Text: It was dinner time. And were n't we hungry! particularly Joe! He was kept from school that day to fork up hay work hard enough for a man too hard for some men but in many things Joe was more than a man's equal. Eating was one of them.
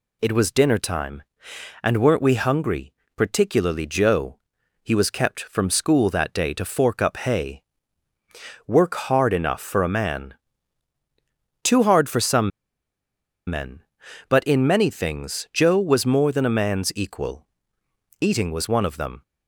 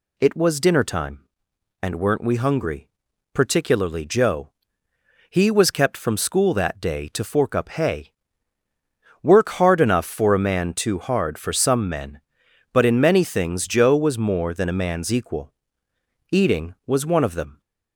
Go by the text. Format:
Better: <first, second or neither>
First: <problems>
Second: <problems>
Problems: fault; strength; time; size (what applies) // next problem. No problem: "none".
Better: second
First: pauses between "hay" and "work"; at 7.6 s; 1.0 s long // pauses between "man" and "too"; strong; at 10.3 s; 1.3 s long // pauses between "some" and "men"; at 12.5 s; 0.99 s long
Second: pauses between "hay" and "work"; at 8.1 s; 1.0 s long